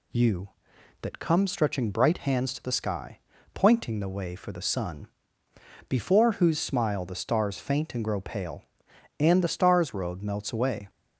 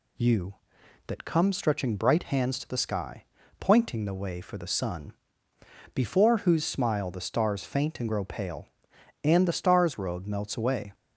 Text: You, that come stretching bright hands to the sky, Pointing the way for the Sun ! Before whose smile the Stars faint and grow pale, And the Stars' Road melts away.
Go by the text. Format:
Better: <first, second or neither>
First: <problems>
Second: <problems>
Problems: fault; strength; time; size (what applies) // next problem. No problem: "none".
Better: neither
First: none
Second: none